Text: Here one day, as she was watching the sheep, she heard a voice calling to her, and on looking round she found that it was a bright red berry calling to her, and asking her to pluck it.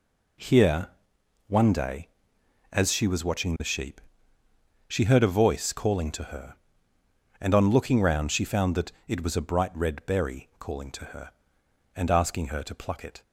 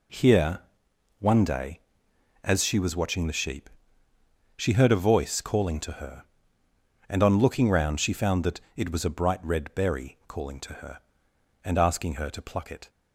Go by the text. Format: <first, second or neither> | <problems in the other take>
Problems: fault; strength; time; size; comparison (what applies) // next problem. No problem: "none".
neither | pauses between "Here" and "one"; noticeable; the same in both // pauses between "that" and "it"; slight; the same in both